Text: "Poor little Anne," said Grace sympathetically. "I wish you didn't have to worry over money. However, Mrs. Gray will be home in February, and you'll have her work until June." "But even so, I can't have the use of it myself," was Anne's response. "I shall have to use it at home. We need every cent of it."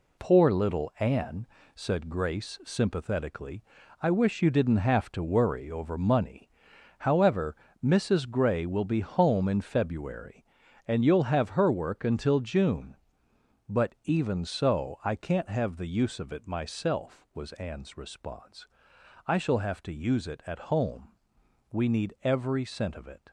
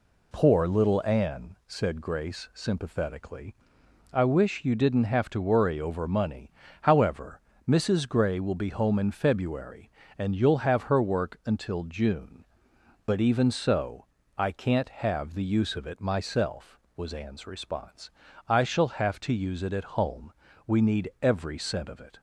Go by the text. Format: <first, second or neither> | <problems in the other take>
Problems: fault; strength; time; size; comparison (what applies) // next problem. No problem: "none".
second | gets quieter; strong; throughout; 7 dB